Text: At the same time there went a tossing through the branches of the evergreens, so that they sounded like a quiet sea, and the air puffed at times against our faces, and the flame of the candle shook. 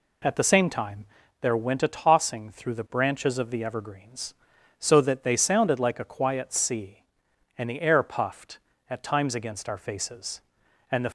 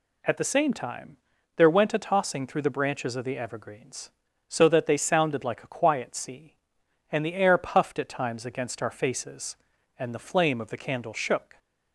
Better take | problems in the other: second | pauses between "time" and "there"; slight; at 1.0 s; 0.36 s long; also in the second // stops before "flame of the candle shook"; at 11.0 s

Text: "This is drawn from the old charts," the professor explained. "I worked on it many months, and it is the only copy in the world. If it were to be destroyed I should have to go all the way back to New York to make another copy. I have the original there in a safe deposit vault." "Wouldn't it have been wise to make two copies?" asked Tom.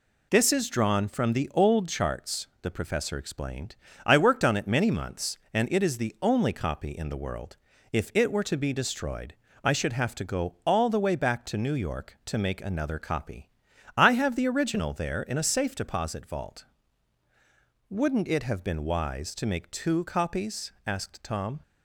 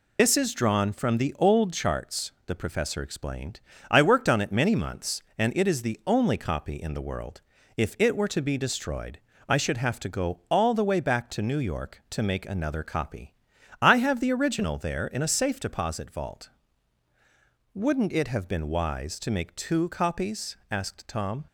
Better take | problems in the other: first | loses the start of "This"; at 0.1 s; 40 ms // pauses between "destroyed" and "I"; slight; at 9.1 s; 0.28 s long; slight in the first

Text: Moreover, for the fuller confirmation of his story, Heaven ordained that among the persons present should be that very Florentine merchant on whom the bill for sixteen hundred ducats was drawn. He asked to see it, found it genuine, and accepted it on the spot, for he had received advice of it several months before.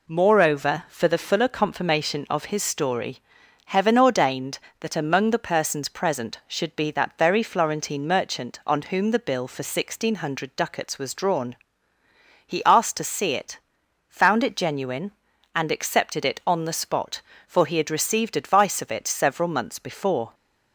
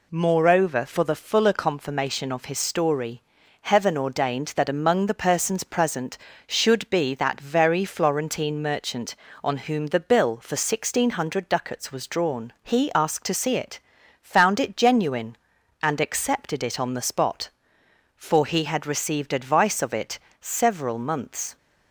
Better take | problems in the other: first | pauses between "it" and "several"; slight; at 20.1 s; 0.20 s long // stops before "before"; at 21.5 s

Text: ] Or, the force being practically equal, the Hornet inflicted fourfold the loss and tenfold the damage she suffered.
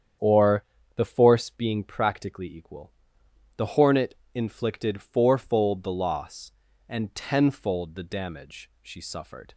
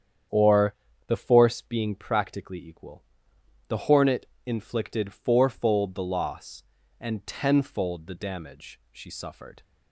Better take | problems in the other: neither | starts louder than the rest; strong; the same in both // pauses between "Hornet" and "inflicted"; slight; the same in both

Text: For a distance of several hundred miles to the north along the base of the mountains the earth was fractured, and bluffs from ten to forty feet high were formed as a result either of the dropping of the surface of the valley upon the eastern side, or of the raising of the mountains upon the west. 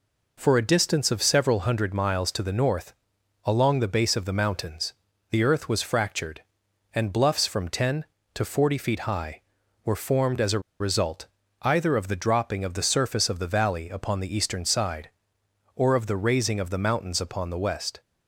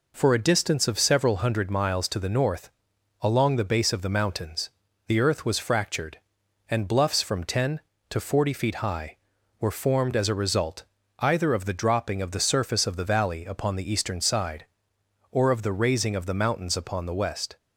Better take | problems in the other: second | pauses between "north" and "along"; noticeable; at 2.9 s; 0.50 s long; noticeable in the second // pauses between "mountains" and "the"; at 4.9 s; 0.38 s long; also in the second // pauses between "a" and "result"; slight; at 10.6 s; 0.20 s long // pauses between "result" and "either"; slight; at 11.2 s; 0.34 s long; slight in the second

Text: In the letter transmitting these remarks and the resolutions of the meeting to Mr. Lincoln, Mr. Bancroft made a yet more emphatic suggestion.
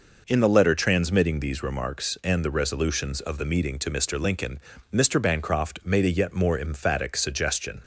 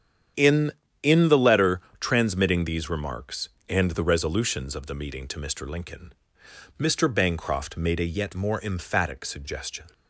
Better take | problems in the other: first | starts louder than the rest; strong; until 1.6 s; 8.5 dB // says "In" twice; at 1.0 s // pauses between "letter" and "transmitting"; slight; at 1.8 s; 0.20 s long

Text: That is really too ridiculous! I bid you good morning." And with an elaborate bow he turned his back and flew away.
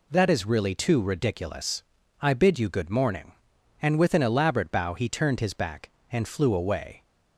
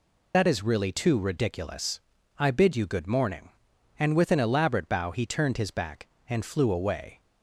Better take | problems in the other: first | loses the start of "That"; at 0.3 s; 75 ms

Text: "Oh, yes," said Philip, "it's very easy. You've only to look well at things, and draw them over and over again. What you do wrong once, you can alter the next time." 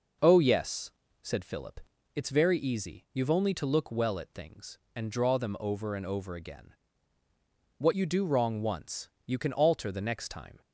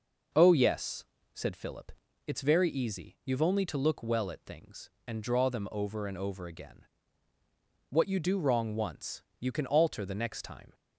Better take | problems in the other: neither | none

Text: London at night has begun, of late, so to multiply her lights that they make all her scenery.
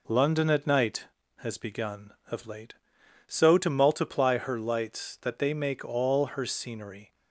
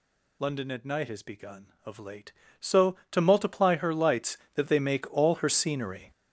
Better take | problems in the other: first | gets louder; strong; throughout; 10.5 dB

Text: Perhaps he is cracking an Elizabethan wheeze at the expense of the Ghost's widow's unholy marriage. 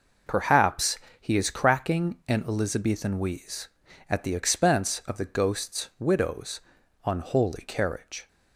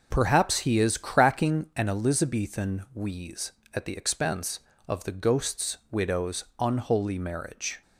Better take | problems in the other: second | pauses between "Perhaps" and "he"; slight; at 0.9 s; 0.24 s long // pauses between "widow's" and "unholy"; noticeable; at 6.5 s; 0.46 s long; slight in the second // says "carriage" for "marriage"; at 7.6 s

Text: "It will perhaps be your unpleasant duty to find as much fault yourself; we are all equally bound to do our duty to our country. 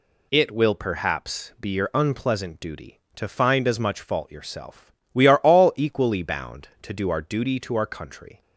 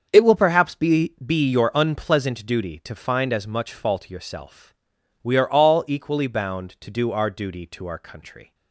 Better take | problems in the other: first | starts louder than the rest; until 1.1 s; 7 dB // says "be" twice; at 1.2 s

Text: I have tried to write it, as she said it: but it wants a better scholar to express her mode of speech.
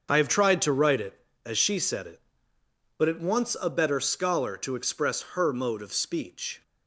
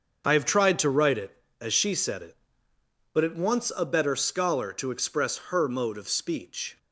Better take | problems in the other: neither | starts louder than the rest; the same in both

